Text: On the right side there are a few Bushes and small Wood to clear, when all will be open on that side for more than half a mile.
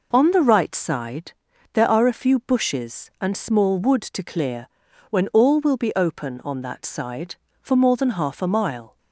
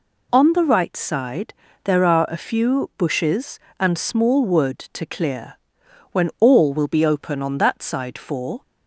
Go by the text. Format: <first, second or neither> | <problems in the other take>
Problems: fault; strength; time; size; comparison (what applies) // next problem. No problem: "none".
first | pauses between "side" and "there"; slight; at 1.5 s; 0.32 s long; also in the first // stops before "more than half a mile"; at 8.6 s